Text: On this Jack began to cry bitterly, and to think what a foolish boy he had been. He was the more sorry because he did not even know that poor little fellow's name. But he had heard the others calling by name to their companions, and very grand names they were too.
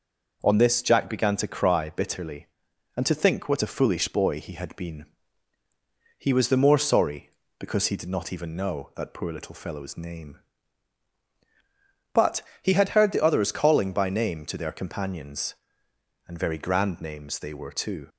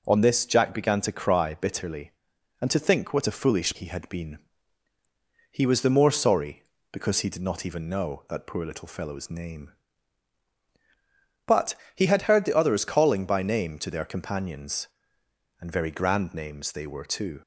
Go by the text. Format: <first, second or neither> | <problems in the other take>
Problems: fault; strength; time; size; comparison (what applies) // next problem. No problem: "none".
first | skips "boy"; at 3.7 s // pauses between "But" and "he"; slight; at 11.7 s; 0.22 s long; slight in the first